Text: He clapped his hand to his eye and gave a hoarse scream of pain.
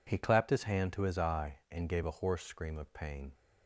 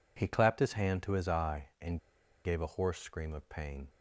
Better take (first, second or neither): first